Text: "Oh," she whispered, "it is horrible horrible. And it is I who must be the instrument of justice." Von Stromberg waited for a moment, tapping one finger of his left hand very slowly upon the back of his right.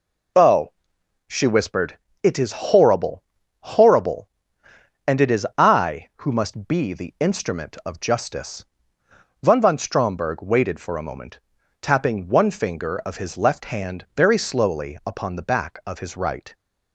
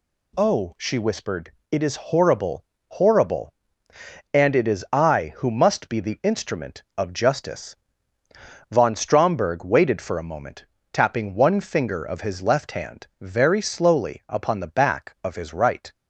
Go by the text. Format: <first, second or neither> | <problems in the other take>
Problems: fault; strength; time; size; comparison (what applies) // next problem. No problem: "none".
second | pauses between "horrible" and "horrible"; at 3.2 s; 0.38 s long; slight in the second // says "Von" twice; at 9.5 s